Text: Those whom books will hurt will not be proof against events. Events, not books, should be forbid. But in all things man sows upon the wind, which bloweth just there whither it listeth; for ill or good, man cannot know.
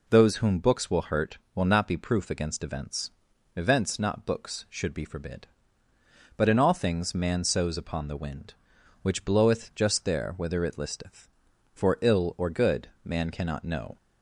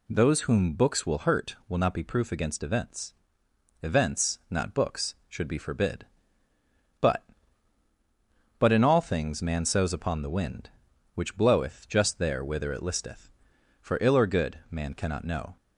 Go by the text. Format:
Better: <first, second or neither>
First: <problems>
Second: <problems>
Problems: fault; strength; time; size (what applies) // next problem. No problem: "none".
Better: first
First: none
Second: says "But" twice; at 8.5 s